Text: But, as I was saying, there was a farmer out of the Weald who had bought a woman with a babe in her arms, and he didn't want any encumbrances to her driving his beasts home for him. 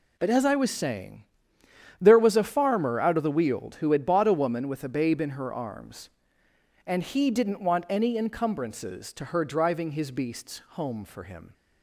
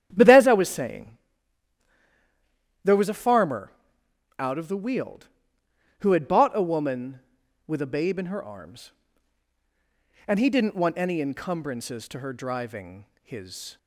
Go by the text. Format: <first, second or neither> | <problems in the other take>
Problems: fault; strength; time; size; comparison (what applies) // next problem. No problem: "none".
first | starts louder than the rest; strong; until 1.1 s; 10 dB // pauses between "farmer" and "out"; noticeable; at 3.7 s; 0.66 s long // pauses between "driving" and "his"; slight; at 13.0 s; 0.18 s long // stops before "beasts home for him"; at 13.7 s